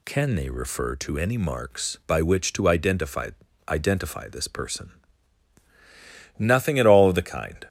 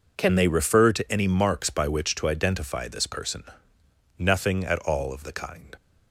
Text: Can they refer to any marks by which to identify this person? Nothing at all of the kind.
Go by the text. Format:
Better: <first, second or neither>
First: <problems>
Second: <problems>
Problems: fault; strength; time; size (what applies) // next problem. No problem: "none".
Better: second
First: says "identify" twice; at 3.6 s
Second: none